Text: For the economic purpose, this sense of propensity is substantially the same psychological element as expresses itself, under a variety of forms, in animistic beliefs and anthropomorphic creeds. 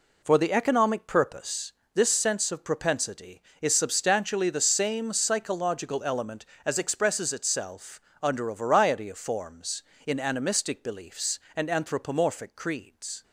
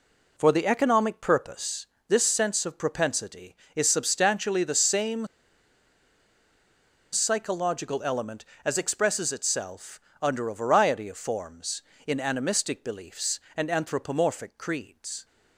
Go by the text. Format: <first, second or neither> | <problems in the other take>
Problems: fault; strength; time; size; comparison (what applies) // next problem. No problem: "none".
first | pauses between "same" and "psychological"; strong; at 5.2 s; 1.8 s long